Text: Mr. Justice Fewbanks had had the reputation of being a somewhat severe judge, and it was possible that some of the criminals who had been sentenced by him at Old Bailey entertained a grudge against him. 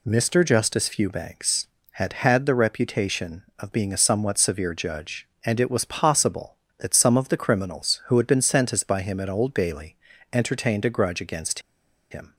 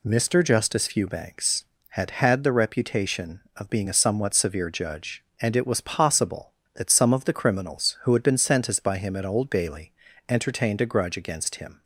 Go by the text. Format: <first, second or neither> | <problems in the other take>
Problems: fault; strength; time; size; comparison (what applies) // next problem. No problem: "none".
second | pauses between "Bailey" and "entertained"; slight; at 9.9 s; 0.34 s long; slight in the second // pauses between "against" and "him"; noticeable; at 11.6 s; 0.50 s long